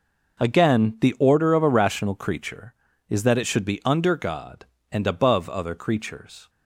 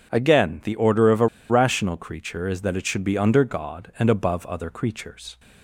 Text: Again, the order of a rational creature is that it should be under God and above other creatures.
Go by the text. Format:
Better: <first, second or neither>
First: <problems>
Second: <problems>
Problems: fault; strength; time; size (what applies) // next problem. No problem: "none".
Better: first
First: none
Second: pauses between "a" and "rational"; slight; at 1.2 s; 0.23 s long